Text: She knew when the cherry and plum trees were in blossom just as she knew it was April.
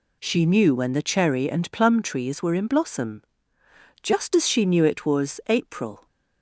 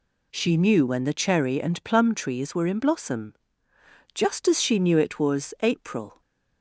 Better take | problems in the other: neither | pauses between "blossom" and "just"; noticeable; the same in both

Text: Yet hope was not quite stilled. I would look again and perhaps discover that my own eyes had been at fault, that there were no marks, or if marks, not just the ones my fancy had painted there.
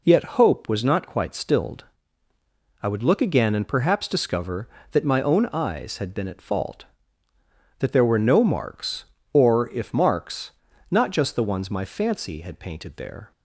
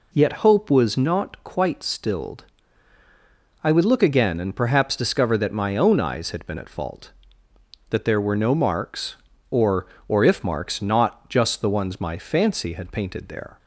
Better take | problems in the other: first | says "or" twice; at 10.0 s

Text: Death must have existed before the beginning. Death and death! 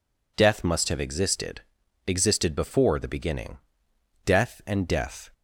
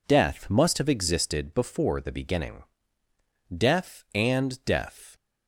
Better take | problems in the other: second | says "existed" twice; at 2.0 s

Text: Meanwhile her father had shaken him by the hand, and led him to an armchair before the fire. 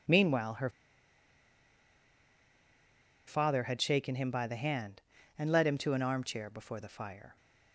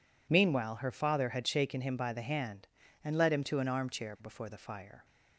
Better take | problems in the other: second | pauses between "her" and "father"; strong; at 0.6 s; 2.5 s long

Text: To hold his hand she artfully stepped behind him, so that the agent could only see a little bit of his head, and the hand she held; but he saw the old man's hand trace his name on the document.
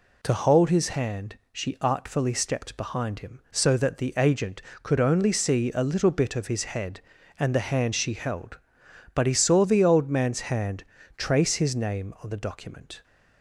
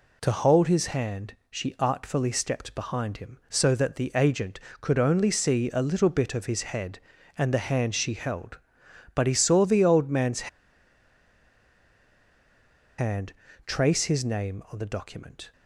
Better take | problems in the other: first | pauses between "man's" and "hand"; strong; at 10.4 s; 2.4 s long // pauses between "hand" and "trace"; slight; at 13.3 s; 0.34 s long; slight in the first

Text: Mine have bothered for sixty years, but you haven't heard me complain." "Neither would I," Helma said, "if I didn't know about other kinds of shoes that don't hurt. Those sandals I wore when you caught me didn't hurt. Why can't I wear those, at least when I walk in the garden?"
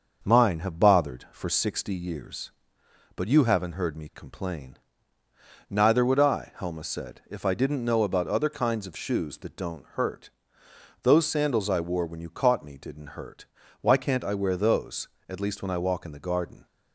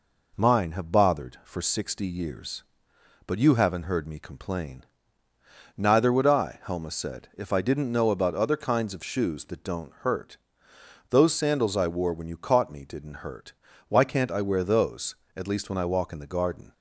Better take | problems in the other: second | starts louder than the rest; until 2.1 s; 6.5 dB

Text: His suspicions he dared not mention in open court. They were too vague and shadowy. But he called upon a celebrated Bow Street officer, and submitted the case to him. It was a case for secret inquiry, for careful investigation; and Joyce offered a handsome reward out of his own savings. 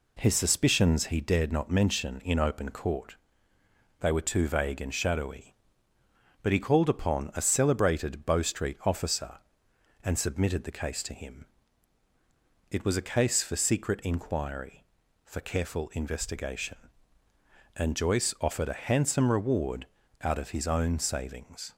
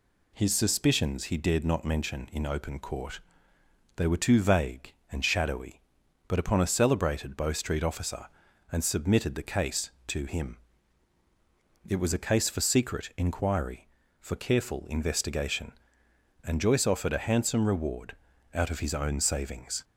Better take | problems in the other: first | skips "he called"; at 6.4 s // pauses between "reward" and "out"; at 18.1 s; 0.38 s long; also in the first

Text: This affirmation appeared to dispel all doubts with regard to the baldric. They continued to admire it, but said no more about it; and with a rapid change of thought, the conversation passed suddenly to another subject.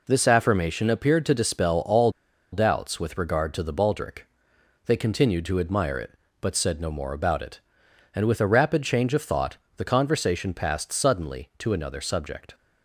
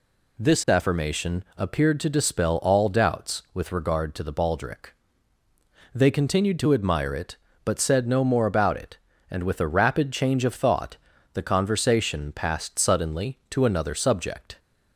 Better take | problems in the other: second | pauses between "all" and "doubts"; at 2.0 s; 0.42 s long

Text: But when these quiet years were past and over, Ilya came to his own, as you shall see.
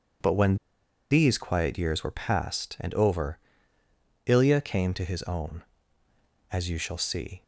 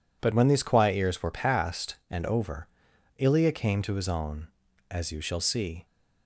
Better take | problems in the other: second | pauses between "when" and "these"; noticeable; at 0.5 s; 0.55 s long

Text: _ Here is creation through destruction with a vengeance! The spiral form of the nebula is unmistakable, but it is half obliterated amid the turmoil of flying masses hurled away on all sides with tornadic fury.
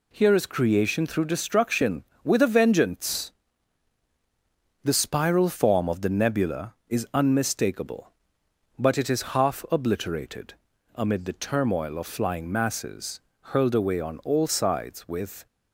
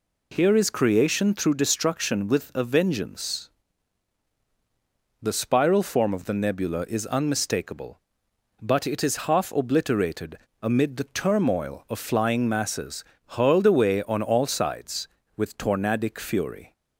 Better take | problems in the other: second | pauses between "obliterated" and "amid"; at 10.5 s; 0.44 s long; slight in the second // pauses between "masses" and "hurled"; slight; at 13.2 s; 0.30 s long; slight in the second // stops before "tornadic fury"; at 15.4 s

